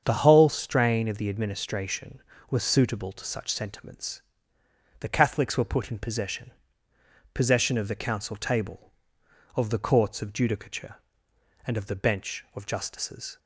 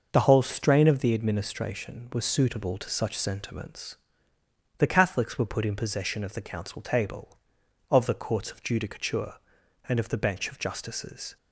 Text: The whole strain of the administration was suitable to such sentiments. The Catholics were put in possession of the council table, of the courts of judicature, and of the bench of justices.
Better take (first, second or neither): second